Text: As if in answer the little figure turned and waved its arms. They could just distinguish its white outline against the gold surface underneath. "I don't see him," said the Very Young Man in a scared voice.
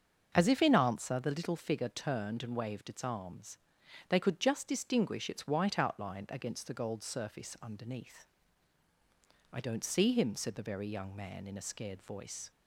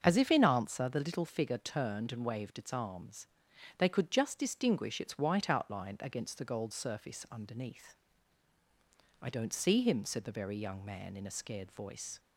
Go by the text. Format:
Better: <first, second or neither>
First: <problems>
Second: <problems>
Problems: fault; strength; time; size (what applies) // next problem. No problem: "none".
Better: neither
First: starts louder than the rest; until 1.3 s; 6.5 dB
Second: starts louder than the rest; until 1.0 s; 6.5 dB